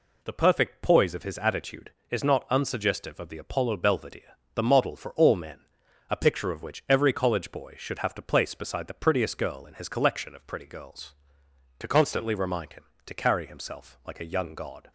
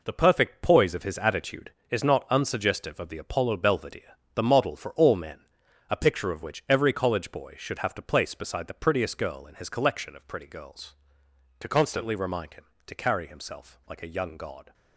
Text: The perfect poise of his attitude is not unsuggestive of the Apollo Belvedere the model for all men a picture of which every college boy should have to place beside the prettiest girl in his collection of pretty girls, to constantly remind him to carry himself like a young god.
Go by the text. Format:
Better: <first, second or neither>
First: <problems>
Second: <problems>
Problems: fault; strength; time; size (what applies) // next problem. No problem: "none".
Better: first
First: pauses between "Belvedere" and "the"; slight; at 4.3 s; 0.18 s long // pauses between "men" and "a"; noticeable; at 5.6 s; 0.48 s long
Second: gets quieter; strong; throughout; 7.5 dB // pauses between "Belvedere" and "the"; slight; at 4.1 s; 0.18 s long // pauses between "men" and "a"; noticeable; at 5.4 s; 0.48 s long